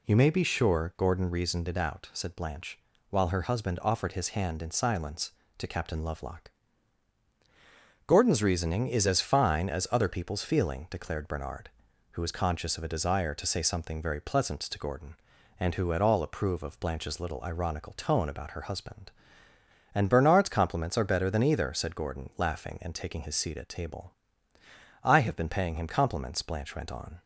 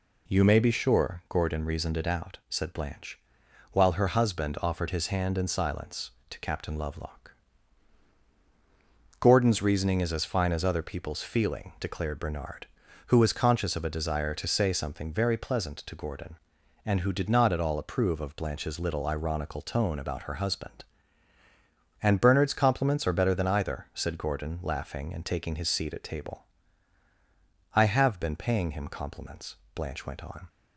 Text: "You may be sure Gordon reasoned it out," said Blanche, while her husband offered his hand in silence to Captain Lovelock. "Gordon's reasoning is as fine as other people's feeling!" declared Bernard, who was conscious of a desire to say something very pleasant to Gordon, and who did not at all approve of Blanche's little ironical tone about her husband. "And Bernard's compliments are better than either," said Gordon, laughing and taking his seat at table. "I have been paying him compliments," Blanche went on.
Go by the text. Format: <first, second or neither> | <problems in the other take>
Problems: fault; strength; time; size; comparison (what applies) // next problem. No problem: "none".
second | skips "did not"; at 15.9 s